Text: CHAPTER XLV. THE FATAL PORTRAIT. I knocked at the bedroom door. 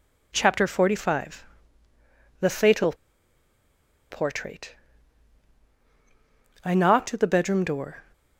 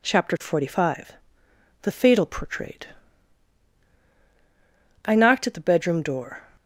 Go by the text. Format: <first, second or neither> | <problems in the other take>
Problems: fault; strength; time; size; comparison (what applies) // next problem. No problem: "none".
second | pauses between "FATAL" and "PORTRAIT"; at 2.9 s; 1.1 s long